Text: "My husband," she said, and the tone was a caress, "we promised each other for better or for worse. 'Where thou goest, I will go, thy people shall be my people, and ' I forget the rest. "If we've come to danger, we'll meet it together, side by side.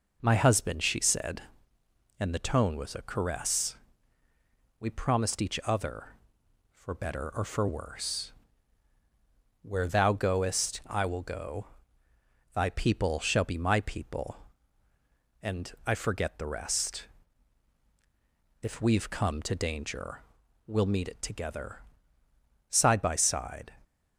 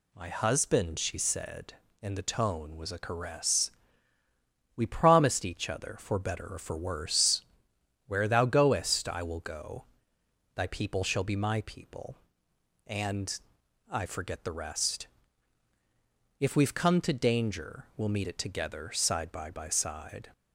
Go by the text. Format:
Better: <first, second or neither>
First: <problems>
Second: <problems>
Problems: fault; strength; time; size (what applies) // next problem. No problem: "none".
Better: first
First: none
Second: says "by" twice; at 19.5 s